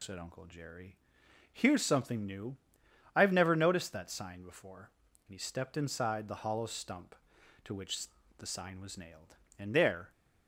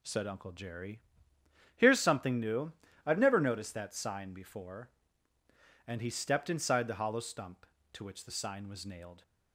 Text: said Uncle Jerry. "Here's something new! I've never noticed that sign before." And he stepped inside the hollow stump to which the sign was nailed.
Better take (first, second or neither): second